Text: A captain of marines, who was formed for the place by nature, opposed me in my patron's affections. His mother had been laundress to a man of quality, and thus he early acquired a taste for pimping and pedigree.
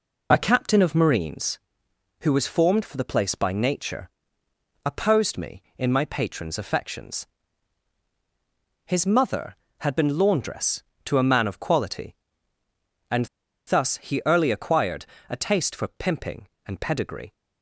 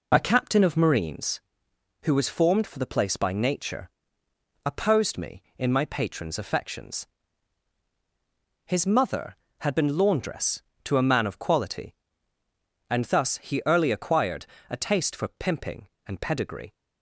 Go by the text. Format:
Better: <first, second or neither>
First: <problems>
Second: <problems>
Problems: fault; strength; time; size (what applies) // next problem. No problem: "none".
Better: second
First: pauses between "and" and "thus"; at 13.2 s; 0.41 s long // pauses between "acquired" and "a"; slight; at 15.0 s; 0.22 s long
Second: pauses between "acquired" and "a"; slight; at 14.4 s; 0.22 s long